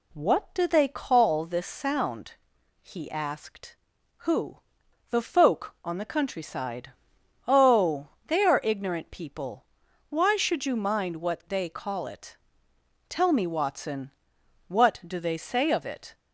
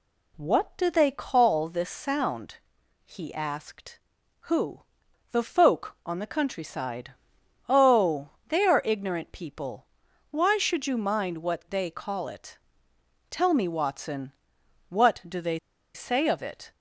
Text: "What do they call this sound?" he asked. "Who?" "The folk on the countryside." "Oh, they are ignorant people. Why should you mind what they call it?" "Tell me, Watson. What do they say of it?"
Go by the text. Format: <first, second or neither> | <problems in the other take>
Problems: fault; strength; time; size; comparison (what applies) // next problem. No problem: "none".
first | pauses between "they" and "say"; at 15.5 s; 0.37 s long